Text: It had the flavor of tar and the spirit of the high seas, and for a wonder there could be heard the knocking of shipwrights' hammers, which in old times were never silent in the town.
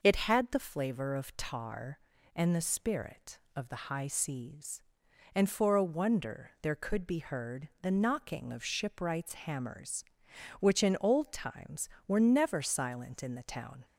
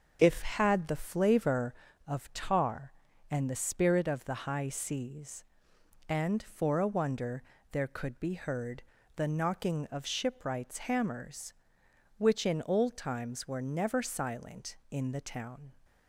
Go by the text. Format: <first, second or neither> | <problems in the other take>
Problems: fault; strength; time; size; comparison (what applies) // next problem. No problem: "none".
first | starts louder than the rest; until 1.2 s; 6.5 dB // says "If" for "It"; at 0.2 s // pauses between "wonder" and "there"; slight; at 7.4 s; 0.28 s long // pauses between "heard" and "the"; slight; at 8.8 s; 0.34 s long